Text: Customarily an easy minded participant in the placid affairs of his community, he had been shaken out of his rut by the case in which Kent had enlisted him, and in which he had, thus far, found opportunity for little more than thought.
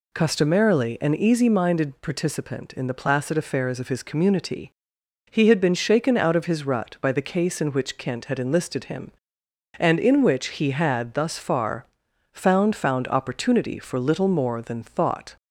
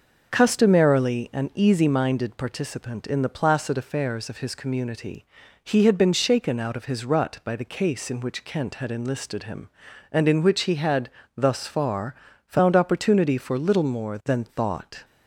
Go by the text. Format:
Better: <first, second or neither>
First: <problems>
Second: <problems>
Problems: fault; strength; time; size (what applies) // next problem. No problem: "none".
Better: second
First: says "found" twice; at 12.7 s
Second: none